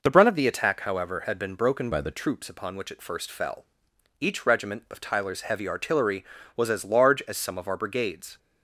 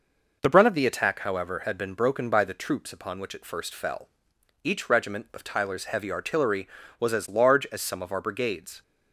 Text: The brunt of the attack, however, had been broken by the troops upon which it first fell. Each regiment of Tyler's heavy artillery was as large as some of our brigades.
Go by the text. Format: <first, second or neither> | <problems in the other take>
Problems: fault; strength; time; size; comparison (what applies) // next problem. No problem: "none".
second | changes voice from "by" to "the"; from 1.9 to 2.1 s; 0.2 s long